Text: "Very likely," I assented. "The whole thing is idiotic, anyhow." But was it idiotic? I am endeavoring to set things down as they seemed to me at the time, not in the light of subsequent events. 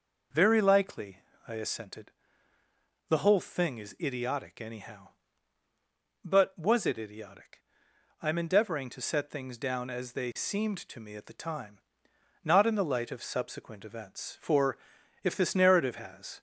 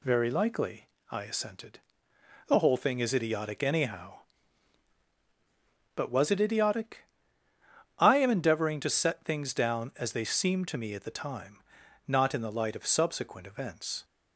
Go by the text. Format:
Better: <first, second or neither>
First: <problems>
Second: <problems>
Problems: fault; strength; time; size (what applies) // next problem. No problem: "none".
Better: second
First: goes on to say "For if this narrative has"; strong; from 14.4 s on; 2.0 s long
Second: none